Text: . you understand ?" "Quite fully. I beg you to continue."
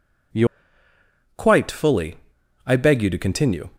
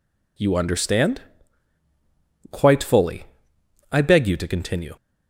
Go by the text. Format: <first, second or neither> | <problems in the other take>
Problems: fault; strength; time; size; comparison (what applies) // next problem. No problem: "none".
second | skips "understand"; at 0.6 s